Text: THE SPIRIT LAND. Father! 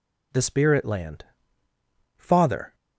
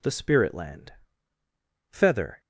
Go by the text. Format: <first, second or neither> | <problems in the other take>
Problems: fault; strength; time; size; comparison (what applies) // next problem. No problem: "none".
first | says "Feather" for "Father"; at 1.9 s